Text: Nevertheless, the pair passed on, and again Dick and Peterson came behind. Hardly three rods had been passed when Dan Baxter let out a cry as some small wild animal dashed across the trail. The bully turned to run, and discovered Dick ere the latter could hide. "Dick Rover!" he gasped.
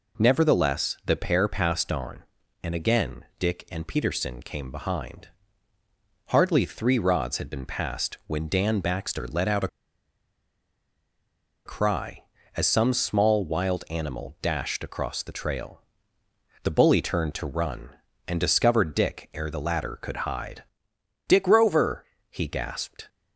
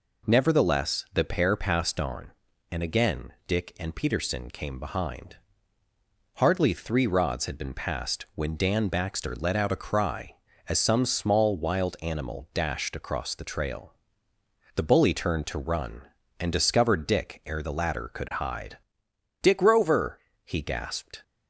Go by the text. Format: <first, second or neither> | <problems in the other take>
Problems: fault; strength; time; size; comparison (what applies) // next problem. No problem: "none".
second | pauses between "a" and "cry"; strong; at 9.6 s; 1.9 s long